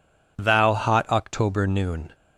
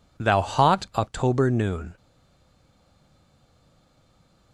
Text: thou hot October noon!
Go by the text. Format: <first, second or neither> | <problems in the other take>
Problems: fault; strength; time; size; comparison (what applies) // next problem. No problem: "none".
first | stays silent after the last word; strong; from 1.9 s on; 2.6 s long